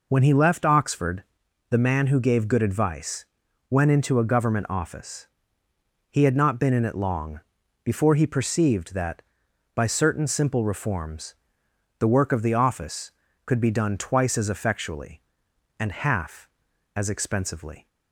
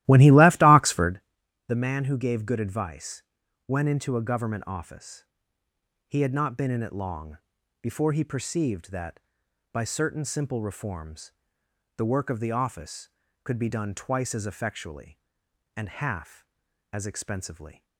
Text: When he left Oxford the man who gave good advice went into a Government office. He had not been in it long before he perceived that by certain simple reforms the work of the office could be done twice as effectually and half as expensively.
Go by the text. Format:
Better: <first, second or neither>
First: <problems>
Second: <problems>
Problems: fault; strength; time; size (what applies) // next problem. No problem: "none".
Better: first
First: pauses between "Oxford" and "the"; noticeable; at 1.2 s; 0.46 s long // pauses between "advice" and "went"; at 3.2 s; 0.42 s long // pauses between "long" and "before"; at 7.4 s; 0.44 s long // pauses between "reforms" and "the"; noticeable; at 11.3 s; 0.64 s long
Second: starts louder than the rest; strong; until 1.2 s; 15.5 dB // pauses between "Oxford" and "the"; noticeable; at 1.1 s; 0.46 s long // pauses between "advice" and "went"; at 3.2 s; 0.42 s long // pauses between "long" and "before"; at 7.3 s; 0.44 s long // pauses between "reforms" and "the"; noticeable; at 11.3 s; 0.64 s long